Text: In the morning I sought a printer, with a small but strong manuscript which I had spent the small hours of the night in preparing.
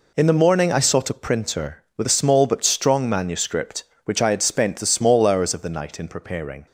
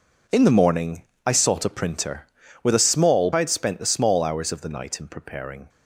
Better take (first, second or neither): first